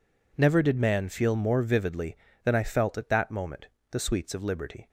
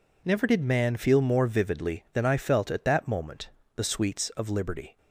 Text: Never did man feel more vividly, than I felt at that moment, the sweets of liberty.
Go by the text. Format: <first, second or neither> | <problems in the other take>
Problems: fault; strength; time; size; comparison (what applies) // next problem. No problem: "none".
neither | none